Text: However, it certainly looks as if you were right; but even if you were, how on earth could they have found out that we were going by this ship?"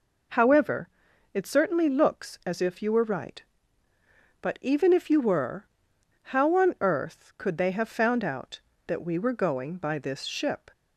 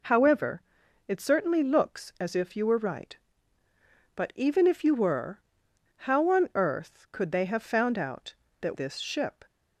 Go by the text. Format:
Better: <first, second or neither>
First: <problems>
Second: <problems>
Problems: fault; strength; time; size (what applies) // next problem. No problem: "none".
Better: first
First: none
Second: skips "we were going by"; at 8.7 s